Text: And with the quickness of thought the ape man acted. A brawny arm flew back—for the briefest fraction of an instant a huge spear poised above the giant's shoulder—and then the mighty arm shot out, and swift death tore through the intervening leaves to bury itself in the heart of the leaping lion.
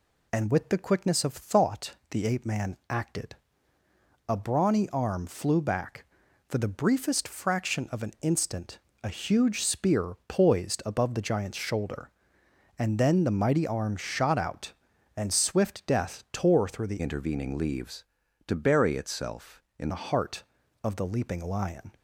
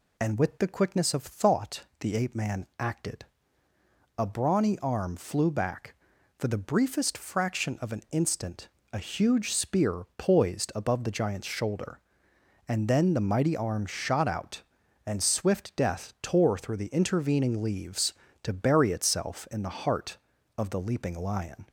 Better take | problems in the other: second | pauses between "thought" and "the"; slight; at 1.9 s; 0.16 s long; slight in the second // pauses between "instant" and "a"; slight; at 8.7 s; 0.24 s long; slight in the second // changes voice from "intervening" to "in"; from 16.9 to 19.8 s; 2.9 s long

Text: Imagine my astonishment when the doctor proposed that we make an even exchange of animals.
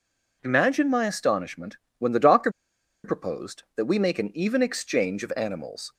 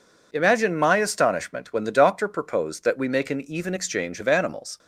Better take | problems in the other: second | pauses between "astonishment" and "when"; slight; at 1.7 s; 0.22 s long // pauses between "doctor" and "proposed"; noticeable; at 2.4 s; 0.54 s long

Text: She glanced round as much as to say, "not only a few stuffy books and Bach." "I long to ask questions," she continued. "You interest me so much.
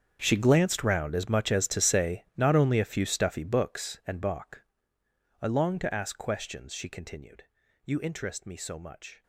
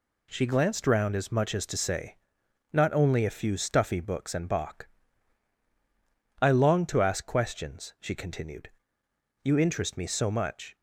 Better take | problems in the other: second | gets quieter; strong; throughout; 18 dB

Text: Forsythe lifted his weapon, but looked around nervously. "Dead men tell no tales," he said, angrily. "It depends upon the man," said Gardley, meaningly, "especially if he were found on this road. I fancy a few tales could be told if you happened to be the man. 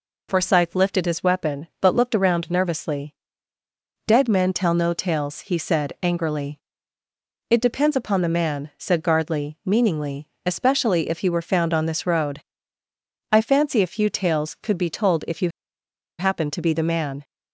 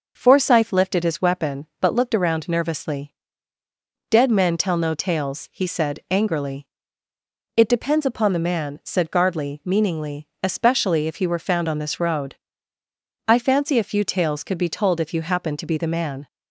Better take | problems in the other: second | pauses between "you" and "happened"; noticeable; at 15.4 s; 0.69 s long

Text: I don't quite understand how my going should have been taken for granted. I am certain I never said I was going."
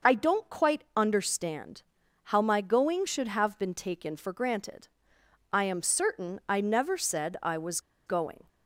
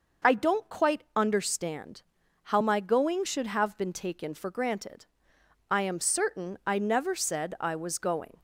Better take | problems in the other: second | pauses between "understand" and "how"; at 1.8 s; 0.42 s long; also in the second // pauses between "was" and "going"; slight; at 7.7 s; 0.27 s long

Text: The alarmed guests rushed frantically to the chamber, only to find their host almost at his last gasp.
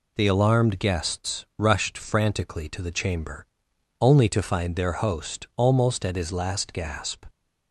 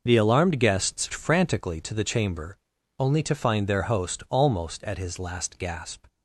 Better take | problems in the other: first | skips "rushed"; at 1.1 s

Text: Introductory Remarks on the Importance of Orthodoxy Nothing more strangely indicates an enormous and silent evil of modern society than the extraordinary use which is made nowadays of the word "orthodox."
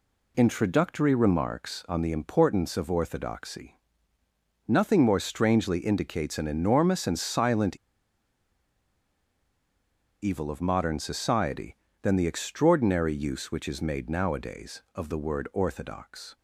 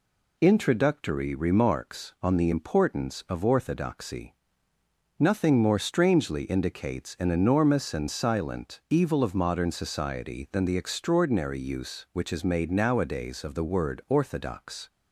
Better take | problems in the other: second | pauses between "Orthodoxy" and "Nothing"; noticeable; at 3.7 s; 0.88 s long; noticeable in the second // pauses between "silent" and "evil"; strong; at 7.7 s; 2.4 s long

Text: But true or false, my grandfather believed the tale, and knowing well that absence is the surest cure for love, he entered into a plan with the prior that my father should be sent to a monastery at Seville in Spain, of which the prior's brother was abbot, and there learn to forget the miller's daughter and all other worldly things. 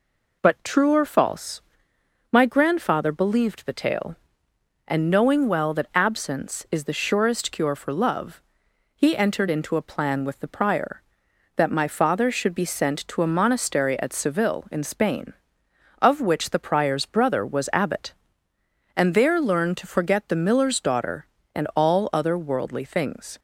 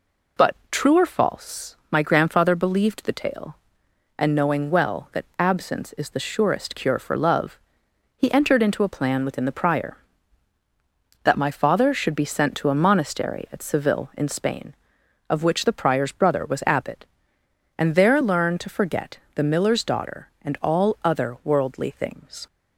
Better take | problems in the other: first | says "within" for "with"; at 9.2 s // pauses between "forget" and "the"; slight; at 19.1 s; 0.16 s long

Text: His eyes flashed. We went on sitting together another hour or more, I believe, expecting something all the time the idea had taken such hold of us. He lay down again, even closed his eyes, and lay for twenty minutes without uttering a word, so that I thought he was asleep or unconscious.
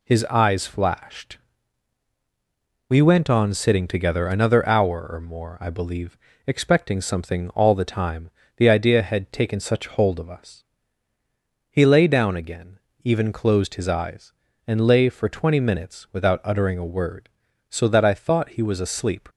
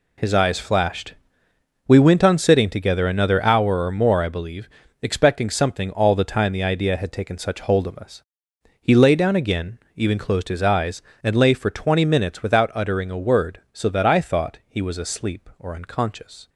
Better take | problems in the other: second | pauses between "time" and "the"; slight; at 8.2 s; 0.28 s long // stops before "or unconscious"; at 19.2 s

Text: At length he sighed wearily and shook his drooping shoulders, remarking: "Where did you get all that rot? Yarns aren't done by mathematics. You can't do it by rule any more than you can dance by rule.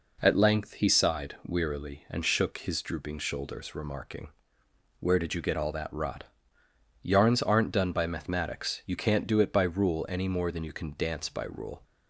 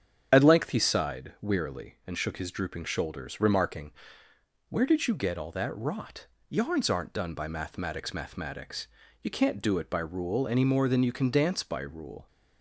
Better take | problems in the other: first | starts louder than the rest; strong; until 1.4 s; 8 dB // says "mathematics" twice; at 8.1 s

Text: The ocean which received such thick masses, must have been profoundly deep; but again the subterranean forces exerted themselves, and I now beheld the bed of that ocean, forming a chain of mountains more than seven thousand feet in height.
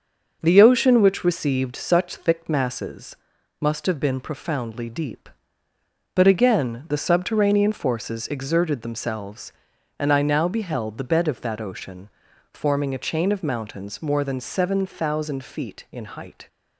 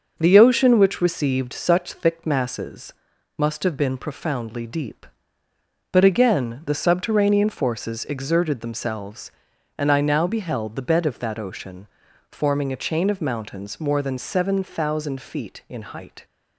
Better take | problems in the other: neither | starts louder than the rest; noticeable; the same in both

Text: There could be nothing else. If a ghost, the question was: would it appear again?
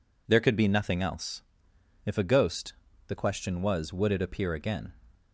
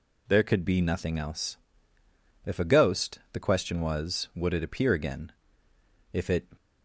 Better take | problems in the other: first | goes on to say "If it"; slight; from 6.1 s on; 0.34 s long

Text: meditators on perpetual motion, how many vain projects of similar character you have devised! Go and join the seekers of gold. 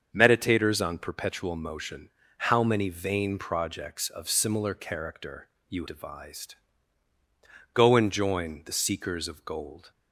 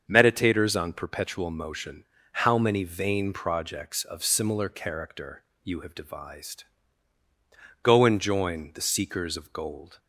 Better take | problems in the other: second | starts louder than the rest; until 1.1 s; 7 dB; also in the second // pauses between "character" and "you"; slight; at 5.4 s; 0.20 s long; slight in the second // skips "have"; at 5.8 s

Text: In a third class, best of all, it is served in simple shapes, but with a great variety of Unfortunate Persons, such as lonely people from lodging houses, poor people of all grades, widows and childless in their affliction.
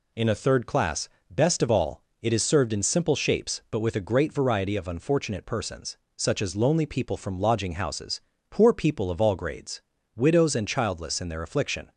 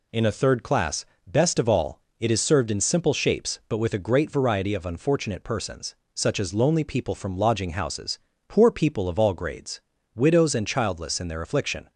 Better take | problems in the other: neither | none

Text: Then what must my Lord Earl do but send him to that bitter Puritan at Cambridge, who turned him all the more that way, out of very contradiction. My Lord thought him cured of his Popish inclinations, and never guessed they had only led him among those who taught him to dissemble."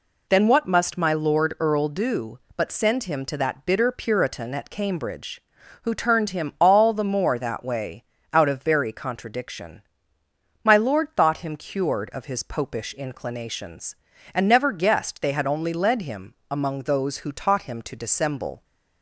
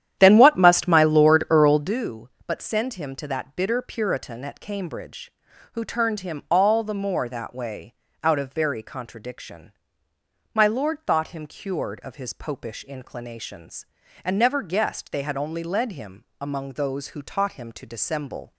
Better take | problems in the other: first | starts louder than the rest; strong; until 2.0 s; 10.5 dB // pauses between "him" and "among"; slight; at 16.2 s; 0.16 s long; slight in the first

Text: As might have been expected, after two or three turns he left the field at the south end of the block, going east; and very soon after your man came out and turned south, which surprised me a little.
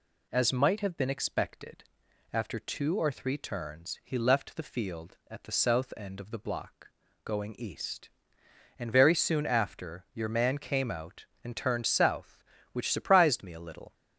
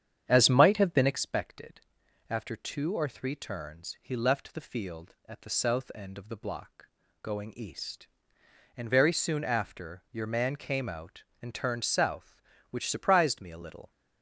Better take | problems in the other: first | starts louder than the rest; strong; until 1.2 s; 9 dB

